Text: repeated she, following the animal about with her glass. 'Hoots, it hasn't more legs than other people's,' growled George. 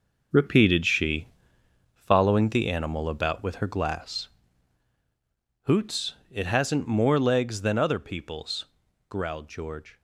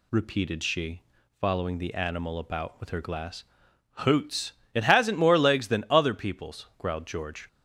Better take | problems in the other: second | gets quieter; strong; throughout; 8.5 dB

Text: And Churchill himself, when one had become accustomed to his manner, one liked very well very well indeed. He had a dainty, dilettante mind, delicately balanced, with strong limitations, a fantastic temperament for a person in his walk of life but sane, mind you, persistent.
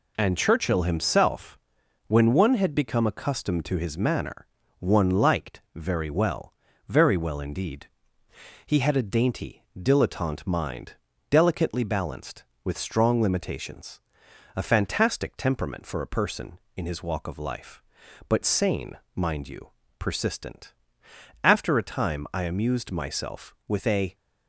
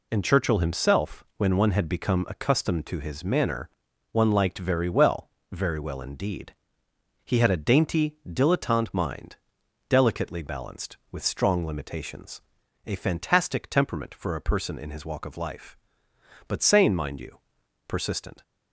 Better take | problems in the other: second | pauses between "well" and "very"; slight; at 6.5 s; 0.36 s long; slight in the second // goes on to say "After a time I amused myself with a"; strong; from 21.4 s on; 2.7 s long

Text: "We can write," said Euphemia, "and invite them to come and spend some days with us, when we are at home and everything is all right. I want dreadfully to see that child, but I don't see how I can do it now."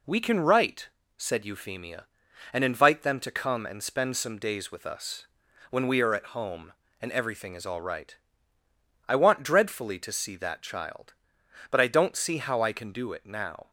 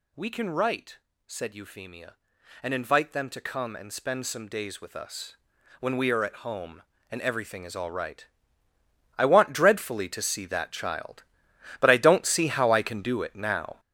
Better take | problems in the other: first | gets louder; strong; throughout; 9 dB

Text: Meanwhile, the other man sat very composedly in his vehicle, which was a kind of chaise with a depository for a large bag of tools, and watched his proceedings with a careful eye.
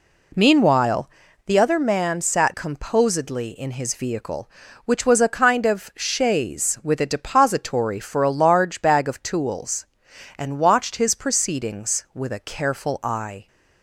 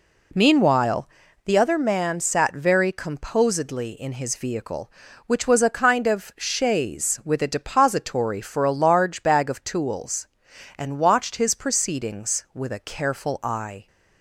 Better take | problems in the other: second | skips "very"; at 2.5 s

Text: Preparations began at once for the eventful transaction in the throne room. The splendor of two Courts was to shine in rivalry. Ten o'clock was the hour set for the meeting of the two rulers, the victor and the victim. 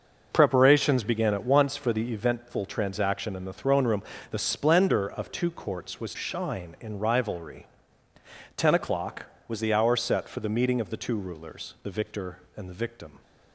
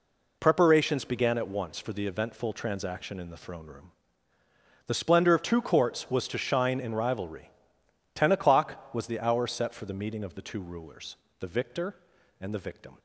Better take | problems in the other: second | skips "to"; at 6.1 s

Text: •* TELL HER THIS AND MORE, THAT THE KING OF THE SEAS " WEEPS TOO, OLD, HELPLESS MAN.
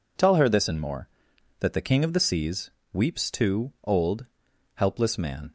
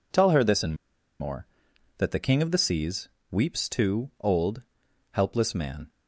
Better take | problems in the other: first | pauses between "AND" and "MORE"; at 0.7 s; 0.44 s long

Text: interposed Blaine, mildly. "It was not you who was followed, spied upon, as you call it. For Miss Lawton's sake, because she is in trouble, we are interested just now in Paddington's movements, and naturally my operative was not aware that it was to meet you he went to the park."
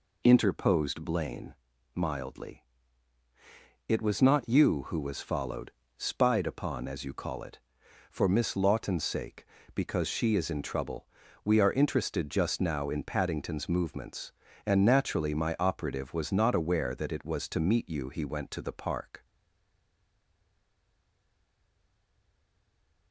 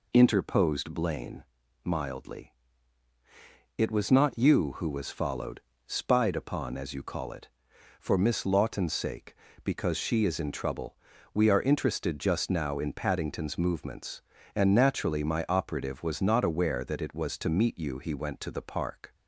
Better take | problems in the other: second | stays silent after the last word; strong; from 19.2 s on; 3.9 s long

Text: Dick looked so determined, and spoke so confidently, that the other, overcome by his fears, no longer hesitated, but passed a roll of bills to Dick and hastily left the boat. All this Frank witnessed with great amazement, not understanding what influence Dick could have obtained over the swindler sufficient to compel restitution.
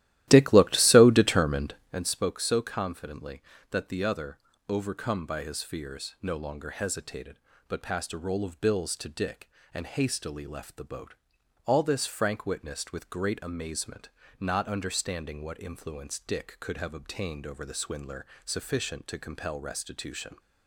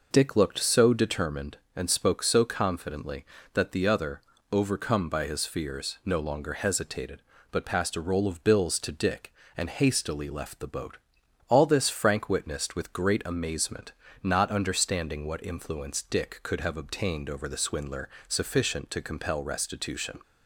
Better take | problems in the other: second | starts louder than the rest; strong; until 2.1 s; 14.5 dB // pauses between "swindler" and "sufficient"; slight; at 18.2 s; 0.20 s long; slight in the second

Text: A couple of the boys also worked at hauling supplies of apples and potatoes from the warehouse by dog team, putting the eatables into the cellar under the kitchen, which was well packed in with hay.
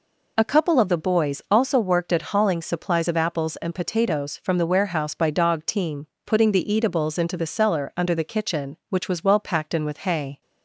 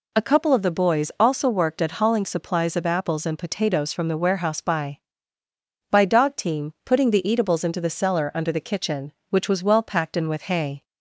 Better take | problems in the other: first | says "by" twice; at 5.9 s

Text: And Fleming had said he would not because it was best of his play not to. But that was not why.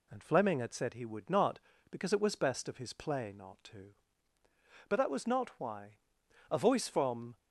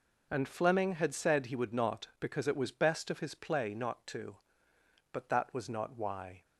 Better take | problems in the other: second | goes on to say "A voice from"; noticeable; from 6.4 s on; 0.88 s long

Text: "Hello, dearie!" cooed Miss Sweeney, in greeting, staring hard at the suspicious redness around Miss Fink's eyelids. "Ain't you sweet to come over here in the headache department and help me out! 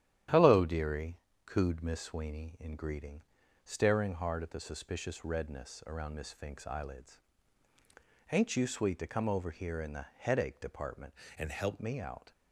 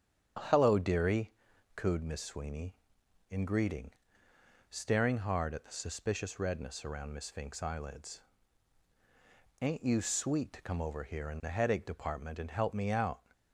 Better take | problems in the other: second | starts louder than the rest; strong; until 1.5 s; 10.5 dB; strong in the second // changes voice from "and" to "help"; from 11.3 to 11.7 s; 0.4 s long

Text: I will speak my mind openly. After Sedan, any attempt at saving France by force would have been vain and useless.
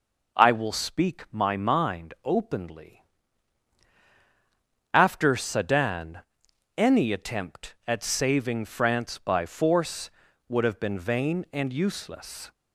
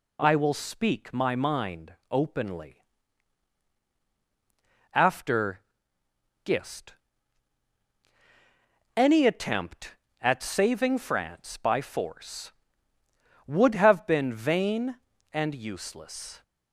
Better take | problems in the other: first | pauses between "mind" and "openly"; slight; at 1.9 s; 0.16 s long // says "Gist" for "Sedan"; at 6.4 s

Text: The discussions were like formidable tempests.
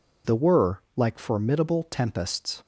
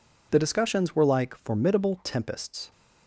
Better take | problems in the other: second | skips "discussions"; at 0.3 s

